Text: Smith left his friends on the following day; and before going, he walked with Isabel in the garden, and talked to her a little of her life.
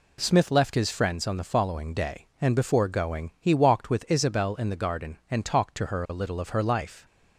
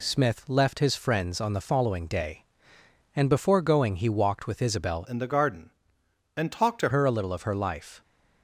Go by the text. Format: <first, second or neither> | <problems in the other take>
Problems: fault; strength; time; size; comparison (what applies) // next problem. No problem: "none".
first | changes voice from "in" to "to"; from 5.0 to 6.8 s; 1.8 s long